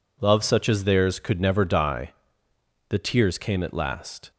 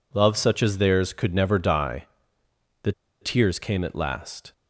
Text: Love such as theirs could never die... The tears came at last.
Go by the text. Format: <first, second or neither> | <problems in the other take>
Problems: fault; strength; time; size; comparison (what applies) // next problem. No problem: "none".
first | pauses between "The" and "tears"; slight; at 2.9 s; 0.30 s long